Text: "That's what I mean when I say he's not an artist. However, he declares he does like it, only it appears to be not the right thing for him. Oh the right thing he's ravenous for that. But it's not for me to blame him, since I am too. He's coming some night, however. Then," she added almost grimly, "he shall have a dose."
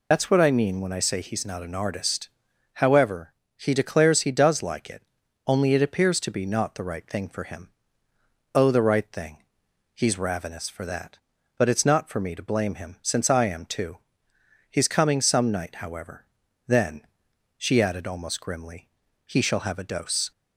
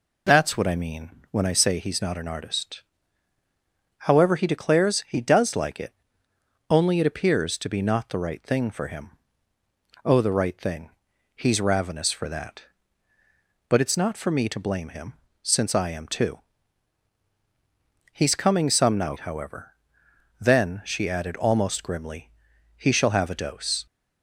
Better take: second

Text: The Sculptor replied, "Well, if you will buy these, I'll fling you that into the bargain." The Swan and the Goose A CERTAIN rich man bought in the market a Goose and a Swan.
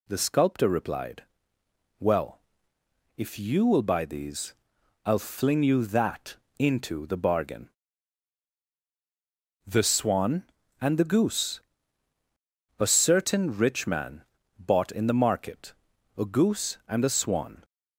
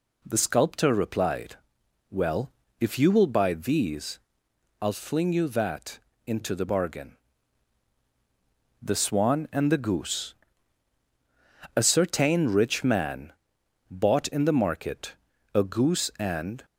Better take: first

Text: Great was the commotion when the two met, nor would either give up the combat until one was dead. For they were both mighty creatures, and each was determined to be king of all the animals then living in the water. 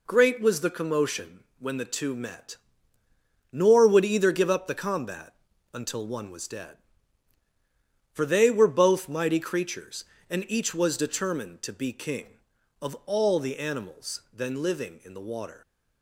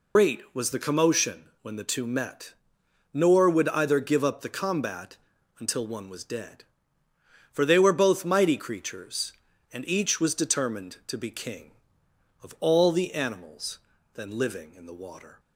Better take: first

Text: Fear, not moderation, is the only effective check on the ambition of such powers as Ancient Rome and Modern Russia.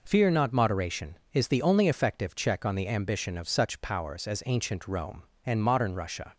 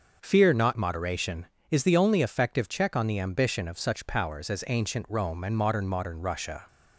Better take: first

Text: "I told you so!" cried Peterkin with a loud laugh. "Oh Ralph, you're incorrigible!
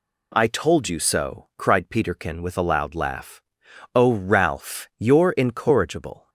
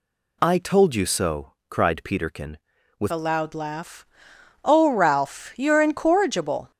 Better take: first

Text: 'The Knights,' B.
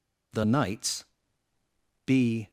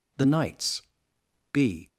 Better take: neither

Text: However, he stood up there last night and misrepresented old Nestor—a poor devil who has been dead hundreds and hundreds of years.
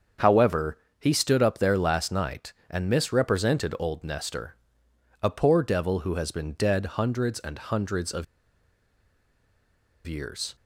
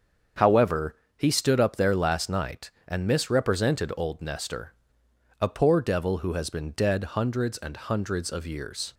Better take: second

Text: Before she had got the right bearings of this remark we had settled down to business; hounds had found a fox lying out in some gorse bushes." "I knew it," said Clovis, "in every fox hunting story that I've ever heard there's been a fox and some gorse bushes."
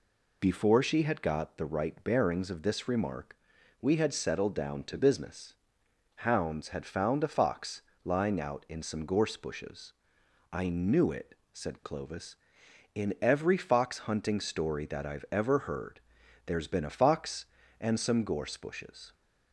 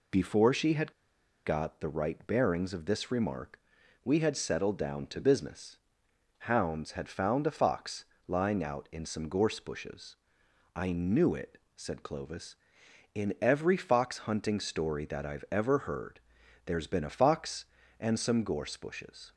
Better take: first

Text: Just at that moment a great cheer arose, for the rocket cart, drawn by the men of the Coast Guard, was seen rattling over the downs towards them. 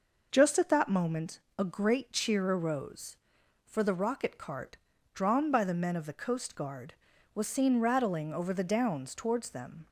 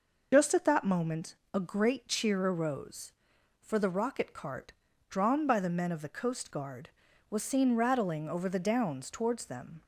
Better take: first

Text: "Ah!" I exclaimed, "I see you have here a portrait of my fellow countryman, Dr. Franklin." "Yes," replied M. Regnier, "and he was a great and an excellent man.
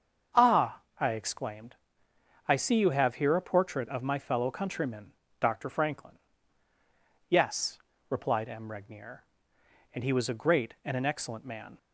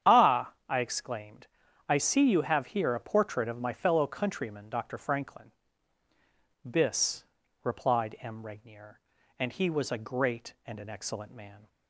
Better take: first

